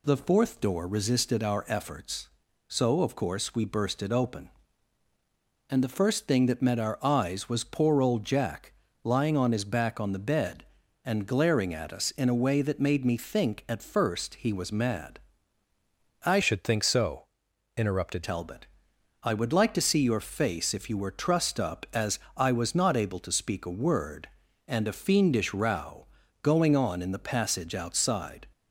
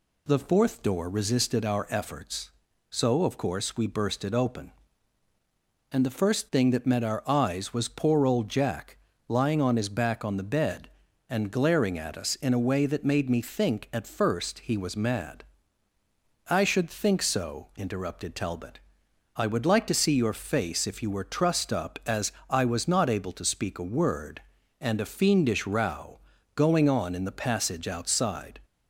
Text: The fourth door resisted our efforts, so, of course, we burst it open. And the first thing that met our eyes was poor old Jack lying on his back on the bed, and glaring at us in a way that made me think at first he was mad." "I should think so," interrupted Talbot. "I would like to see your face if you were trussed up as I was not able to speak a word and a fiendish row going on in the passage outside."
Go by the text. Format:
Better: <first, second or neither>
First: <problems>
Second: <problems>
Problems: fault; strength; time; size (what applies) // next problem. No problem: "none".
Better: second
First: pauses between "Jack" and "lying"; slight; at 8.7 s; 0.30 s long // changes voice from "should" to "interrupted"; from 16.4 to 18.2 s; 1.8 s long // pauses between "as" and "I"; slight; at 22.1 s; 0.16 s long // pauses between "row" and "going"; slight; at 26.0 s; 0.34 s long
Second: pauses between "Jack" and "lying"; slight; at 8.9 s; 0.30 s long // pauses between "as" and "I"; slight; at 22.3 s; 0.16 s long // pauses between "row" and "going"; slight; at 26.1 s; 0.34 s long